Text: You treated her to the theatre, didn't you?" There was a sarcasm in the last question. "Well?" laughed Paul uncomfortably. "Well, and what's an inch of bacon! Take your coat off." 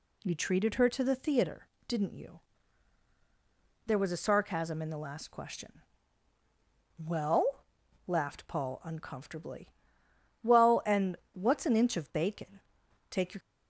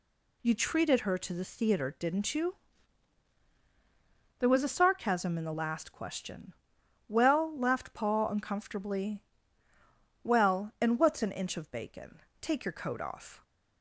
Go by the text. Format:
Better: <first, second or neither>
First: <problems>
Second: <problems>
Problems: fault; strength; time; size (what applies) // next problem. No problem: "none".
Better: second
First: pauses between "and" and "what's"; slight; at 11.1 s; 0.19 s long // stops before "coat off"; at 13.4 s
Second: none